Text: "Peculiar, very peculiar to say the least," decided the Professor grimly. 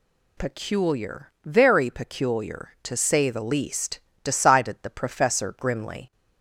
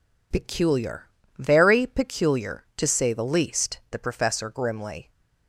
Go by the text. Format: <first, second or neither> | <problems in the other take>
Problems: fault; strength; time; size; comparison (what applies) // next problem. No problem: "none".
first | skips "decided"; at 3.8 s